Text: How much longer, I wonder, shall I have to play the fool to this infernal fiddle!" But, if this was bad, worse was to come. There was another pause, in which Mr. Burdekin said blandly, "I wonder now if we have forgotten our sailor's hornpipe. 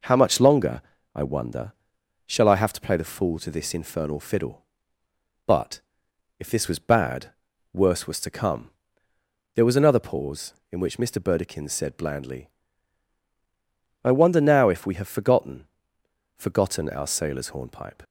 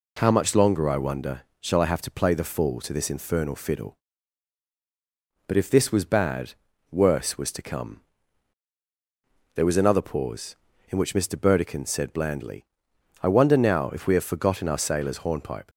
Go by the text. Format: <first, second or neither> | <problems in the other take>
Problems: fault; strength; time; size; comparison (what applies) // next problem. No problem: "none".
second | says "forgotten" twice; at 16.3 s